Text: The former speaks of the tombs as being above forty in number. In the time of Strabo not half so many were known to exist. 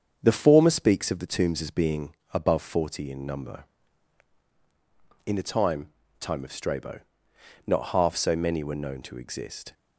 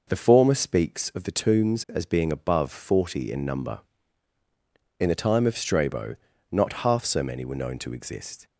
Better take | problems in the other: second | starts louder than the rest; strong; until 1.2 s; 7 dB // pauses between "being" and "above"; slight; at 2.1 s; 0.20 s long // says "time" twice; at 6.1 s // pauses between "Strabo" and "not"; noticeable; at 6.9 s; 0.68 s long; slight in the second

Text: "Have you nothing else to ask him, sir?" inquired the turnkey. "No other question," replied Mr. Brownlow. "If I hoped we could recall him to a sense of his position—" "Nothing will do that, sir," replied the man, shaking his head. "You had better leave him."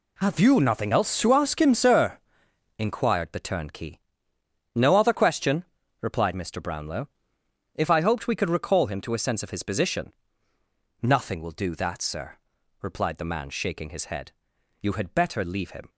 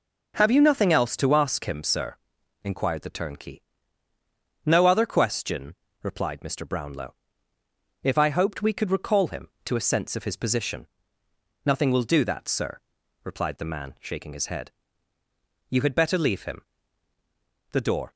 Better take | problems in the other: first | goes on to say "The door"; slight; from 17.7 s on; 0.42 s long

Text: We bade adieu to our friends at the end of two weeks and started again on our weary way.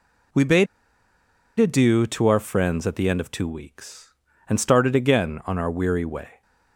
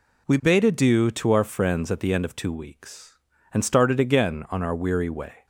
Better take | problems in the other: second | pauses between "bade" and "adieu"; noticeable; at 0.6 s; 0.93 s long

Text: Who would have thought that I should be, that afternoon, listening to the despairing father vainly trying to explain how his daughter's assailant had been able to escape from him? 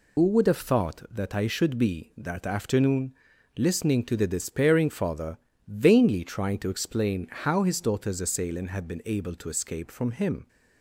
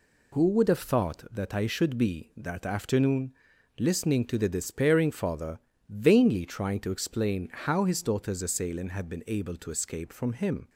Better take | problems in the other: second | loses the start of "Who"; at 0.1 s; 65 ms // pauses between "father" and "vainly"; slight; at 5.3 s; 0.30 s long; slight in the second

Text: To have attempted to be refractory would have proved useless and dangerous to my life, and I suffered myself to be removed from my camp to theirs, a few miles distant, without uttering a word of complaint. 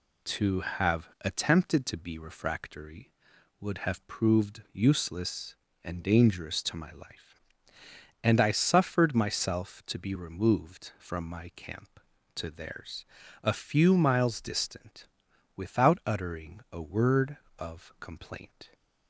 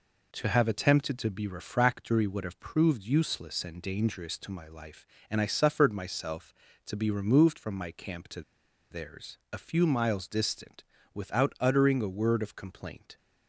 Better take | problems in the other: first | pauses between "to" and "theirs"; noticeable; at 8.4 s; 0.49 s long

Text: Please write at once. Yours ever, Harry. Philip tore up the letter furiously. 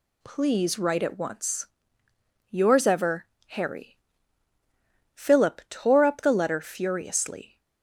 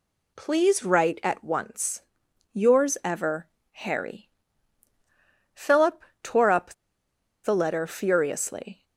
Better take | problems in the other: first | pauses between "Philip" and "tore"; slight; at 6.0 s; 0.20 s long // pauses between "up" and "the"; noticeable; at 6.7 s; 0.69 s long

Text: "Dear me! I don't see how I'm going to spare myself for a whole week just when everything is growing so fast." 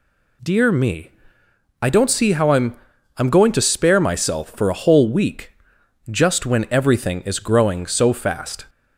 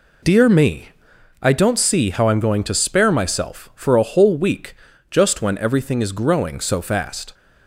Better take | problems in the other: second | says "I'm" twice; at 3.1 s // pauses between "week" and "just"; noticeable; at 5.5 s; 0.58 s long; also in the second

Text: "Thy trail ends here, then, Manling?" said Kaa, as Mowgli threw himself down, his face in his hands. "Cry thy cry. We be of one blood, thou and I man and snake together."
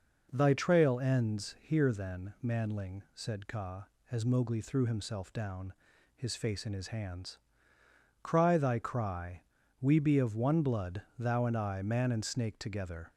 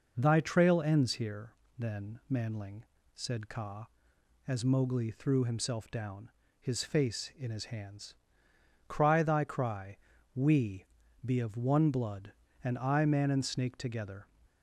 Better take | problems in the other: first | pauses between "We" and "be"; at 10.8 s; 0.40 s long // skips "thou"; at 12.4 s

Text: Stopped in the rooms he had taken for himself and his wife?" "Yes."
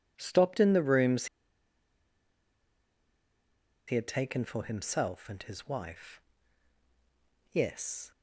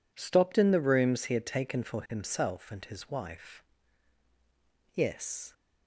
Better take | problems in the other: second | pauses between "rooms" and "he"; strong; at 1.2 s; 2.6 s long

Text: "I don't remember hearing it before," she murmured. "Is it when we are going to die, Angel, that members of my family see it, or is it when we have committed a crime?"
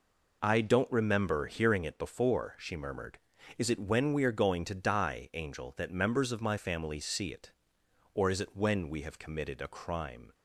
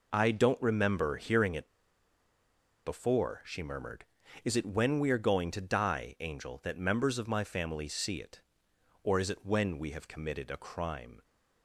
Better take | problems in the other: first | pauses between "it" and "before"; at 1.6 s; 1.1 s long

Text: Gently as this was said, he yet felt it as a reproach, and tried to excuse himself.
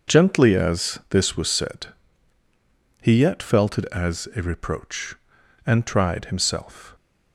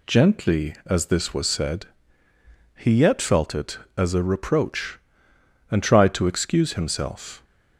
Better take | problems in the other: second | skips "to excuse"; at 6.2 s

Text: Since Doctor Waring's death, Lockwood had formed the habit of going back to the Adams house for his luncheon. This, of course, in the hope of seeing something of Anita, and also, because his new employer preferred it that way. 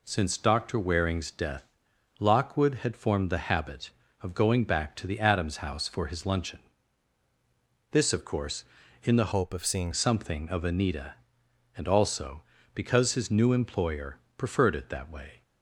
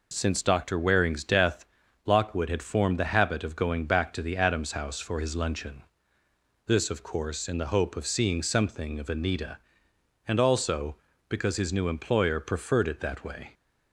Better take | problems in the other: second | changes voice from "hope" to "seeing"; from 9.3 to 9.9 s; 0.6 s long // pauses between "employer" and "preferred"; slight; at 14.1 s; 0.20 s long

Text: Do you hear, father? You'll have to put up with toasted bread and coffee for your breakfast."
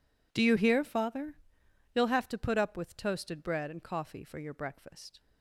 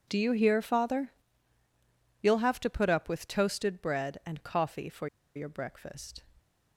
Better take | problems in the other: first | pauses between "for" and "your"; slight; at 5.0 s; 0.29 s long

